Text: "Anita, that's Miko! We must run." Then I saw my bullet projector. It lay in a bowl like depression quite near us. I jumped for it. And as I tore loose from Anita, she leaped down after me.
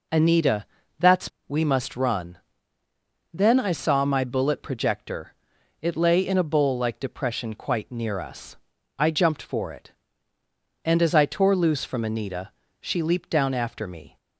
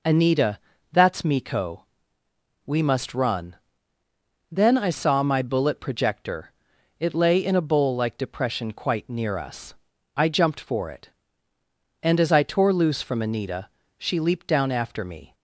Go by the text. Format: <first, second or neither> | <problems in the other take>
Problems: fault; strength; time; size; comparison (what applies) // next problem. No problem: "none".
second | skips "Miko"; at 1.3 s